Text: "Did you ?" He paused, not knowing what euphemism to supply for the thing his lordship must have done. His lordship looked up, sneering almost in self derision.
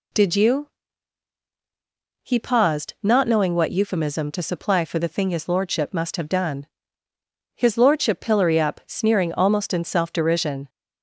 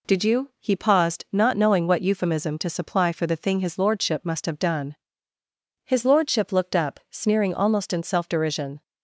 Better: second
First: says "pillory" for "looked"; at 8.2 s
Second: none

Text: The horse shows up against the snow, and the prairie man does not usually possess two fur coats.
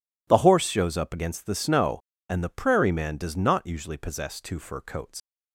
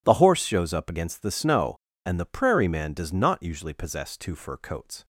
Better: second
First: leaves "coats" unfinished; at 5.1 s; 85 ms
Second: none

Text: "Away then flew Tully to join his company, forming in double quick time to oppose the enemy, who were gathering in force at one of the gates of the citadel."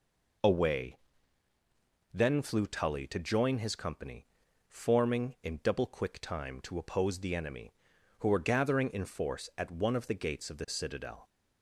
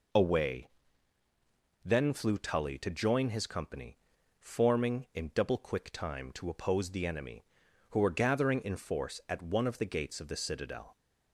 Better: neither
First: pauses between "Away" and "then"; at 0.9 s; 1.1 s long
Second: pauses between "Away" and "then"; at 0.6 s; 1.1 s long

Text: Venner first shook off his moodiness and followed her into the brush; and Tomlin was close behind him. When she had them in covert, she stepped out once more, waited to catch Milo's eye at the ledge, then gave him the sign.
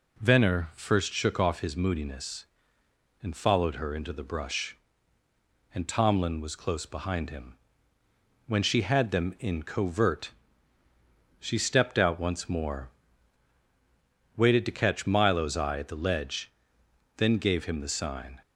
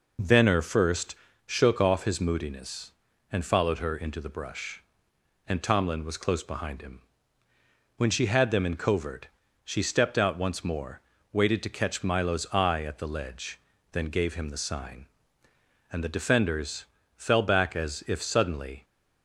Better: first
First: none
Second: pauses between "first" and "shook"; slight; at 1.1 s; 0.30 s long // goes on to say "And the defenders fell back as if suddenly"; strong; from 15.8 s on; 2.9 s long

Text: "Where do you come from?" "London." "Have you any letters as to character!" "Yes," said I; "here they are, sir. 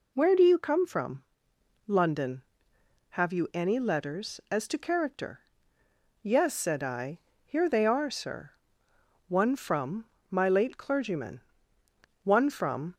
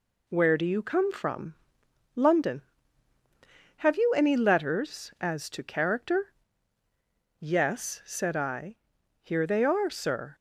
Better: second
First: goes on to say "One from my late clergyman one from"; strong; from 9.2 s on; 3.6 s long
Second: none

